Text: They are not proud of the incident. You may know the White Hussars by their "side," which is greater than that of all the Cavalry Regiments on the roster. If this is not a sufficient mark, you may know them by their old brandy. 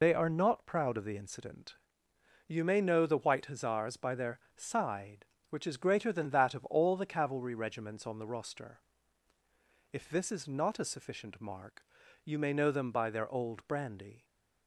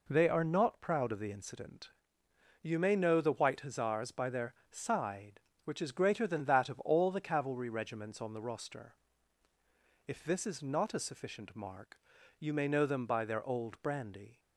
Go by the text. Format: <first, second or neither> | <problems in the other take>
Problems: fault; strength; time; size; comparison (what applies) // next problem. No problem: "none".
second | loses the start of "They"; at 0.0 s; 100 ms // pauses between "their" and "side"; slight; at 4.3 s; 0.18 s long; slight in the second